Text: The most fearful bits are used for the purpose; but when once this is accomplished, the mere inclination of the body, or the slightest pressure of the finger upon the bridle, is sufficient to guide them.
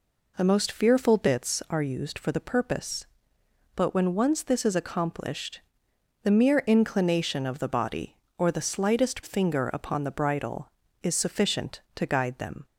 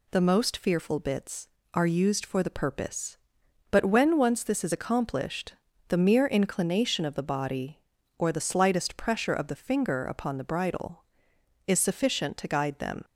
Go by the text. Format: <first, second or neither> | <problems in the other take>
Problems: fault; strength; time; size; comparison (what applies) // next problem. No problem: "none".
second | skips "pressure of the"; at 9.2 s